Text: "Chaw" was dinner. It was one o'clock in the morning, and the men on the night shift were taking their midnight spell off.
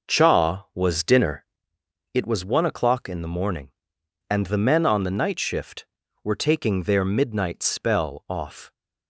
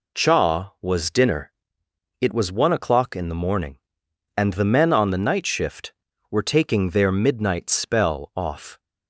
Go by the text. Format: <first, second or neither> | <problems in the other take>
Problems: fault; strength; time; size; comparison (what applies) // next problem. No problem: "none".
second | starts louder than the rest; noticeable; until 1.8 s; 6 dB